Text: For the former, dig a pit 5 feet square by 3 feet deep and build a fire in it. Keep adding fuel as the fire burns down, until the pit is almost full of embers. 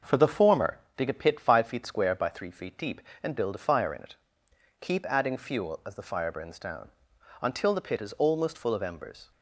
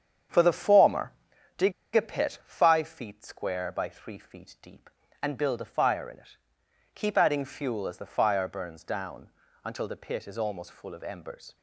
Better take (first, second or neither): first